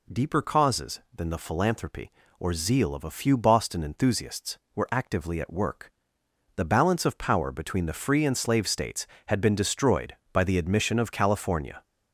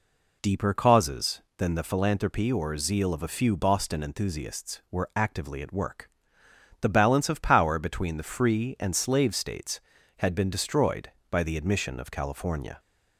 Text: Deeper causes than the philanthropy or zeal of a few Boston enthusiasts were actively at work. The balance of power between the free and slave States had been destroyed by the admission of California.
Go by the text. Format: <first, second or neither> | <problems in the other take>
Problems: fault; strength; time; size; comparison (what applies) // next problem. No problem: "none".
neither | none